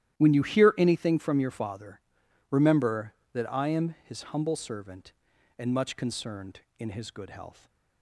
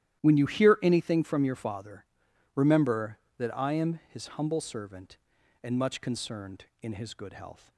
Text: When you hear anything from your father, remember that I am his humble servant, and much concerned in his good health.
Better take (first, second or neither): neither